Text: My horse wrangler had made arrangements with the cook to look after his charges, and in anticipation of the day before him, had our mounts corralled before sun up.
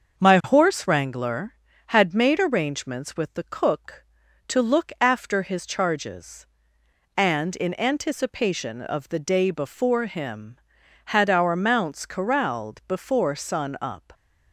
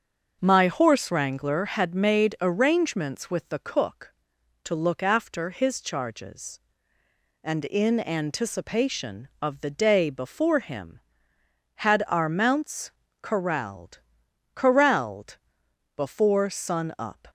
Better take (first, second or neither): first